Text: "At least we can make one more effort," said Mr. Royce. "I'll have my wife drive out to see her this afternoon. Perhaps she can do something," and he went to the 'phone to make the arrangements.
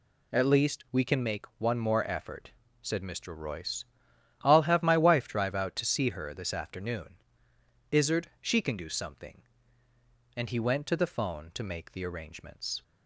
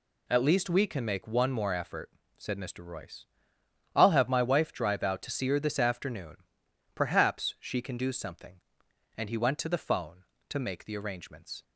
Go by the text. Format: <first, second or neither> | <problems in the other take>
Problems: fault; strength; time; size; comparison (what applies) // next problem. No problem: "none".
second | says "Izzard" for "Perhaps"; at 7.9 s